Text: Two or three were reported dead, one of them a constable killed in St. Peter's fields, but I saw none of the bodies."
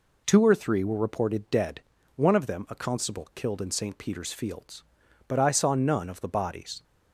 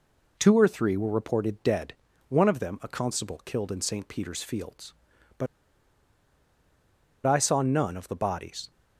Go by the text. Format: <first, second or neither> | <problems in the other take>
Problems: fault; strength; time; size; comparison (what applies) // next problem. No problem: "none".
first | pauses between "but" and "I"; strong; at 5.4 s; 1.7 s long